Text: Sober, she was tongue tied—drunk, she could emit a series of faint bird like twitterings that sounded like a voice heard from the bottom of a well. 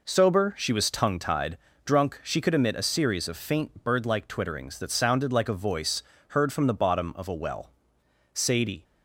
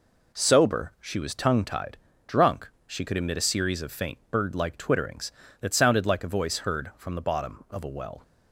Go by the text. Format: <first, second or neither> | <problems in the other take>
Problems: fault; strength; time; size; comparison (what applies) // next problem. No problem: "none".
second | pauses between "voice" and "heard"; slight; at 6.0 s; 0.28 s long // goes on to say "Sadie"; from 8.3 s on; 0.50 s long